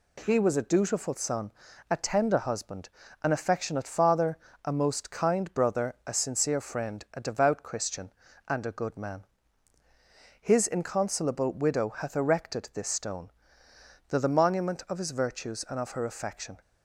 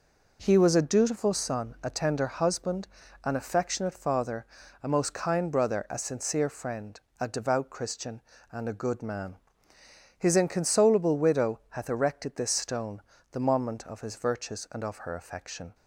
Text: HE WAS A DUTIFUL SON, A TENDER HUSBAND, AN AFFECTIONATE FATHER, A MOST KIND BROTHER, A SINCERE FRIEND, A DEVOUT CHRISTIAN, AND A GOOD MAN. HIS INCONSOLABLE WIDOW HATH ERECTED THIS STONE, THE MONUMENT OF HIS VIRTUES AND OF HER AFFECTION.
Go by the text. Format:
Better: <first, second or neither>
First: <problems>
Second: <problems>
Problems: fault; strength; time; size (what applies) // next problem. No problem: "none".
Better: second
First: says "THE" twice; at 14.1 s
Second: none